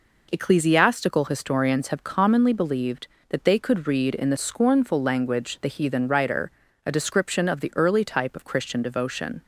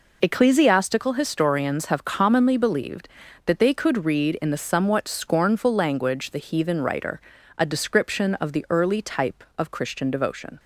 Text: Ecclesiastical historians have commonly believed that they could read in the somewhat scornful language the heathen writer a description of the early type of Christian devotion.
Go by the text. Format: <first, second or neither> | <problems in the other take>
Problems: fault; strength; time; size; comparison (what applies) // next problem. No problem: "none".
second | skips "somewhat"; at 4.3 s // pauses between "writer" and "a"; slight; at 6.5 s; 0.34 s long; slight in the second